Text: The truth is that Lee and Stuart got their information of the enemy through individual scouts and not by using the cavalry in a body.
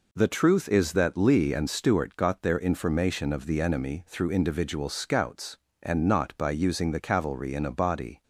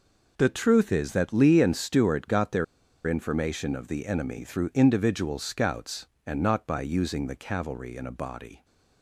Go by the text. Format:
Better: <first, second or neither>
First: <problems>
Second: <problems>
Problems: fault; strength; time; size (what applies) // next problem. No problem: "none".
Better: first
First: none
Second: pauses between "their" and "information"; at 2.6 s; 0.42 s long